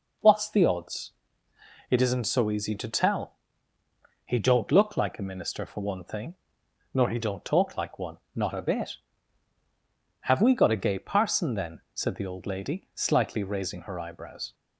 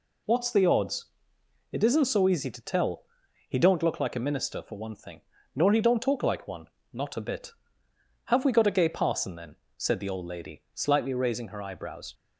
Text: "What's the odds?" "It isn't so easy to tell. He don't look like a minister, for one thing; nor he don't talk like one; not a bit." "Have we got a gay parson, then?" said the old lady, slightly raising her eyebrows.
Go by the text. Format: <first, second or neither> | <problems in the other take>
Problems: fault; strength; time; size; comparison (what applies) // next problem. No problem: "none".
neither | none